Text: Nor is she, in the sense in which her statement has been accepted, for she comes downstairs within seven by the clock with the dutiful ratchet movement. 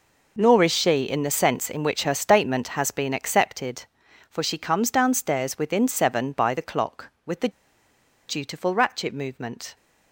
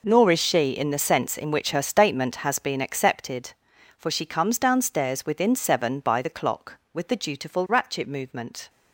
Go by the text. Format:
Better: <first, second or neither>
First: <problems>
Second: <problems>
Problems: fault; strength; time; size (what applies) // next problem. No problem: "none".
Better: second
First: pauses between "the" and "dutiful"; noticeable; at 7.4 s; 0.79 s long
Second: none